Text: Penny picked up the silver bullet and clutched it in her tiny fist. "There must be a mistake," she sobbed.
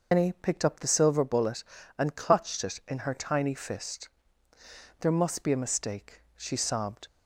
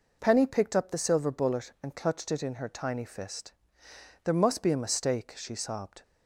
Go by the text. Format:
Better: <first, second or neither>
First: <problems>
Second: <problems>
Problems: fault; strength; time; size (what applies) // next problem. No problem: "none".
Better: second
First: loses the start of "Penny"; at 0.1 s; 155 ms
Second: none